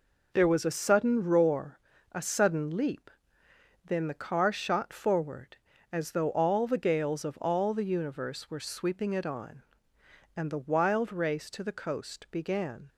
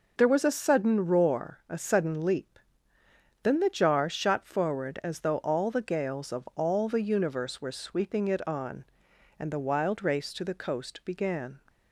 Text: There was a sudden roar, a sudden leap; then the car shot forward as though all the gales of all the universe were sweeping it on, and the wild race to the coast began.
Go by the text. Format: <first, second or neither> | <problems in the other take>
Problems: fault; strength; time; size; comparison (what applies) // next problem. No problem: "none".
first | says "jar" for "car"; at 3.6 s